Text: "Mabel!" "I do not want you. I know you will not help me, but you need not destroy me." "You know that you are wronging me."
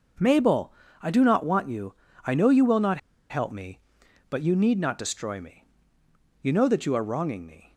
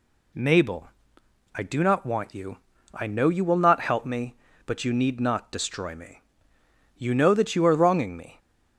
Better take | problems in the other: second | pauses between "not" and "help"; slight; at 2.9 s; 0.32 s long

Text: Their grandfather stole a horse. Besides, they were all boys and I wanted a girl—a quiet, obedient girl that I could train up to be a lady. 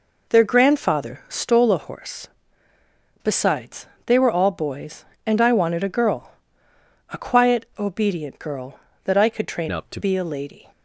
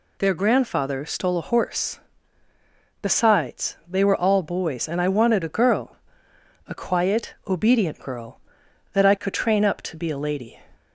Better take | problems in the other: second | changes voice from "up" to "to"; from 9.7 to 9.9 s; 0.2 s long

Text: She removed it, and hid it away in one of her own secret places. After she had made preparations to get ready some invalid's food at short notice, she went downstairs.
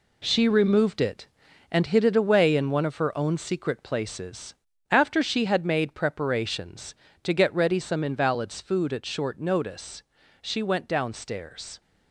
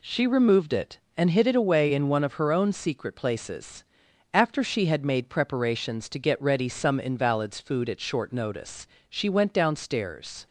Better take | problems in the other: second | gets quieter; strong; throughout; 8 dB

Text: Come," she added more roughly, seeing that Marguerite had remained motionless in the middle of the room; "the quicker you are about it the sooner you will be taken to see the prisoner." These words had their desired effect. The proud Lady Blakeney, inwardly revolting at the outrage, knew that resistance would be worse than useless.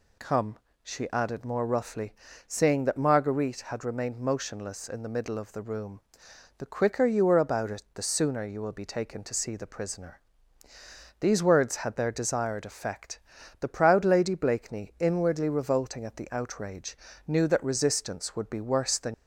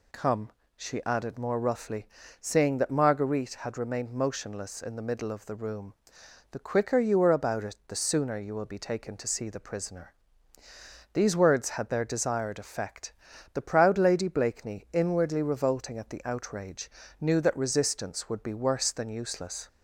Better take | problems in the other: second | stops before "useless"; at 19.1 s

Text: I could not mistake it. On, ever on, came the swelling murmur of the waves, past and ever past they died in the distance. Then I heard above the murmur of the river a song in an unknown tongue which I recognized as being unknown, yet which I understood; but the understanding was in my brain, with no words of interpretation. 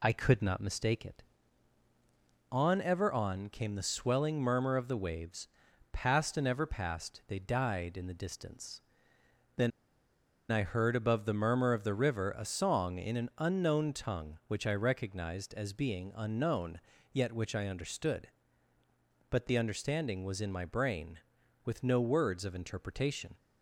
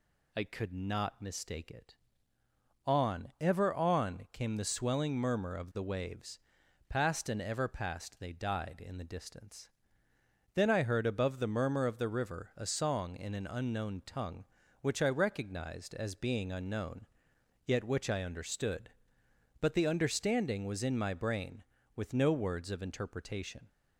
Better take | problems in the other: second | pauses between "Then" and "I"; noticeable; at 9.7 s; 0.79 s long

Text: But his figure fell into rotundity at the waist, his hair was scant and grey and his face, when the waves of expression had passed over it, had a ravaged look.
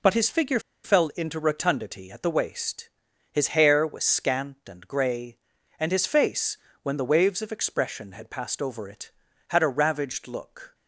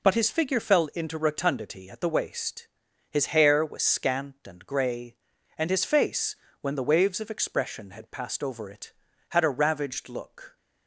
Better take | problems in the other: second | pauses between "figure" and "fell"; slight; at 0.6 s; 0.23 s long

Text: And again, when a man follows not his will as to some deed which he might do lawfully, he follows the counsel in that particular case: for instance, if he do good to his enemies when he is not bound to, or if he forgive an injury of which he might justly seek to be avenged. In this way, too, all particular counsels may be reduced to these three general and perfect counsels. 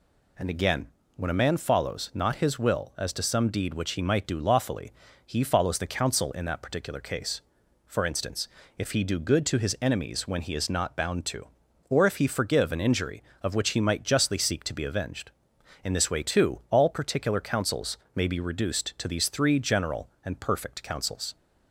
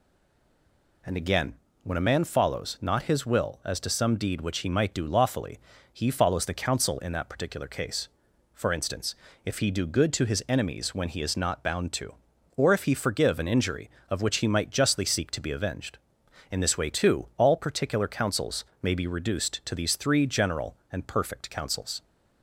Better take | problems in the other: first | stays silent before the first word; until 1.0 s; 1.0 s long // pauses between "counsels" and "may"; slight; at 18.6 s; 0.18 s long; slight in the first

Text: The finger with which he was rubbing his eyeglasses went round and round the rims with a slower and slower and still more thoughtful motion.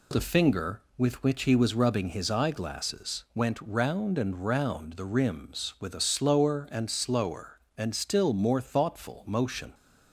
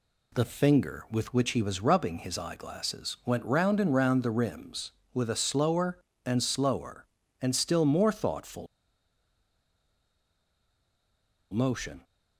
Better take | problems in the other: first | pauses between "thoughtful" and "motion"; strong; at 8.6 s; 2.8 s long

